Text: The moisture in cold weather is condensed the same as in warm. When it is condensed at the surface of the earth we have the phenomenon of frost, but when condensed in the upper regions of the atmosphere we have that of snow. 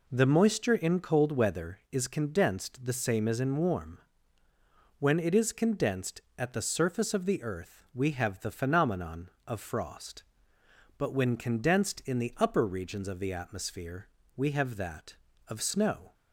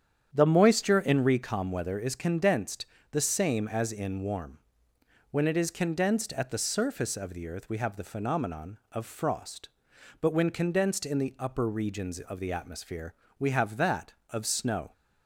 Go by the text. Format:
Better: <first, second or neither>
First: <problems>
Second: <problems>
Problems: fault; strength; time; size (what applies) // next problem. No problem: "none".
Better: first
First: pauses between "atmosphere" and "we"; slight; at 14.0 s; 0.30 s long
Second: starts louder than the rest; strong; until 1.3 s; 8.5 dB // says "recom" for "cold"; at 1.2 s // pauses between "condensed" and "the"; slight; at 2.8 s; 0.28 s long // pauses between "atmosphere" and "we"; slight; at 13.1 s; 0.24 s long